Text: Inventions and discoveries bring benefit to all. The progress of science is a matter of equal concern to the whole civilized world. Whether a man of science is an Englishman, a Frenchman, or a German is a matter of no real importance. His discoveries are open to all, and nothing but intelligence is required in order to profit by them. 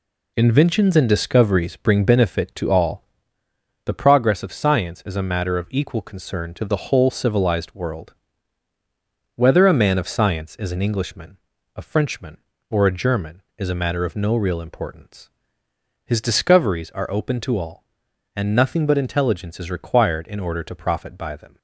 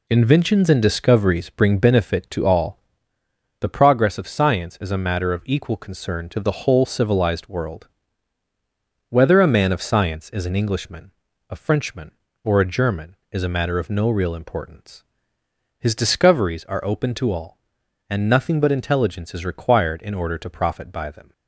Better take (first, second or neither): neither